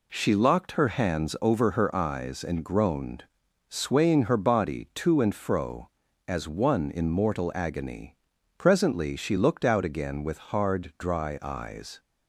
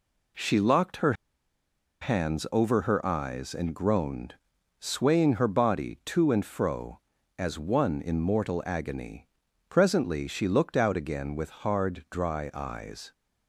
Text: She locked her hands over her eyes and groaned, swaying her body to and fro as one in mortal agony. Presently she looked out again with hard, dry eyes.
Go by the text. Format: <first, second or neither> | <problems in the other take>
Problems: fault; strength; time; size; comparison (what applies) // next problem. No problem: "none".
first | pauses between "her" and "hands"; noticeable; at 1.1 s; 0.88 s long